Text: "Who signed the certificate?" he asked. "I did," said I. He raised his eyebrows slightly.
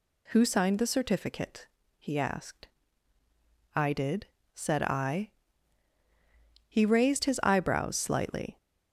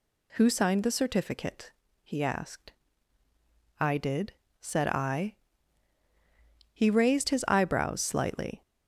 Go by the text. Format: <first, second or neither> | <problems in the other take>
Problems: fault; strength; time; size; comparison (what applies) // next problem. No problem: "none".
neither | none